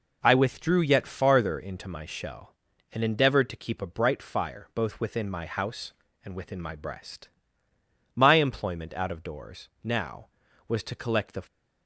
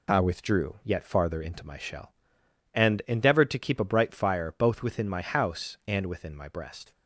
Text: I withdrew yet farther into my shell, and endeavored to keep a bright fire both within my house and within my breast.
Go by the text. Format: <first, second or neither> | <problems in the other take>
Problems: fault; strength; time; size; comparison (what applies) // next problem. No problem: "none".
second | goes on to say "My employment out of doors now was to collect the"; strong; from 8.1 s on; 3.2 s long